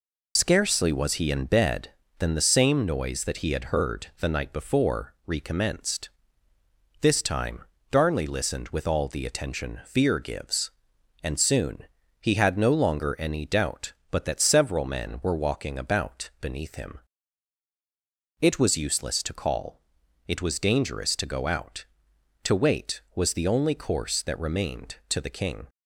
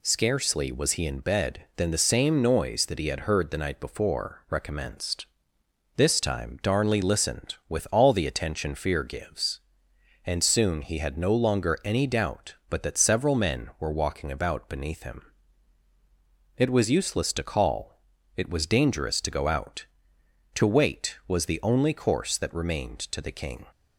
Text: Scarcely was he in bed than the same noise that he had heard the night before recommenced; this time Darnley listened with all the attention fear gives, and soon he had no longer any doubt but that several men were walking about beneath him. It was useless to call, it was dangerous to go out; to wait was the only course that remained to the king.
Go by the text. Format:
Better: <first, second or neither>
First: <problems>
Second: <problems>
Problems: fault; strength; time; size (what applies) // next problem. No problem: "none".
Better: second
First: loses the start of "Scarcely"; at 0.3 s; 70 ms // pauses between "time" and "Darnley"; slight; at 7.6 s; 0.28 s long // pauses between "soon" and "he"; slight; at 11.8 s; 0.36 s long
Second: none